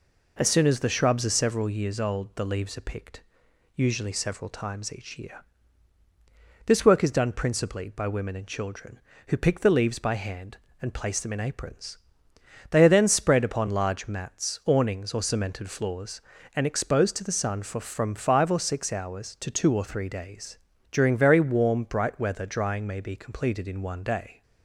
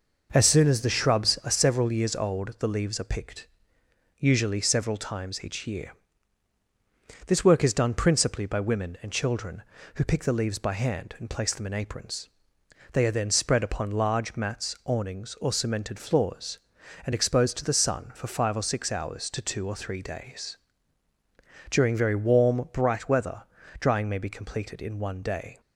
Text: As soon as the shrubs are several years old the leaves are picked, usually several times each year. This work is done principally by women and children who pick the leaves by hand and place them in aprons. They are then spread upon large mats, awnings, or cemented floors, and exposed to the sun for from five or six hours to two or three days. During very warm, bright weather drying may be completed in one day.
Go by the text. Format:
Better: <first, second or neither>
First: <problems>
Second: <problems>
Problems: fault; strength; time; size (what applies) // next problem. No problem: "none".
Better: first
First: none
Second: skips "from"; at 18.2 s // pauses between "weather" and "drying"; at 23.4 s; 0.38 s long